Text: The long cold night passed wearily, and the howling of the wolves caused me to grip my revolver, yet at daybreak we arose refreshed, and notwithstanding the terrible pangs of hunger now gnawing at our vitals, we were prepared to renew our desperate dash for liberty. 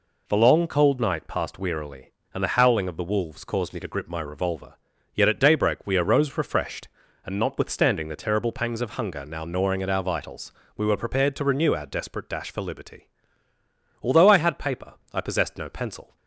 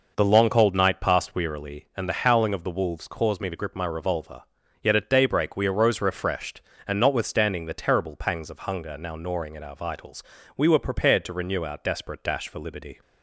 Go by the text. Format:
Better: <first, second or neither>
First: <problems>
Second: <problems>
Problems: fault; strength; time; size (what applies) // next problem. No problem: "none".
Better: second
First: goes on to say "Although I had paper I possessed no pencil"; strong; from 14.0 s on; 2.1 s long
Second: none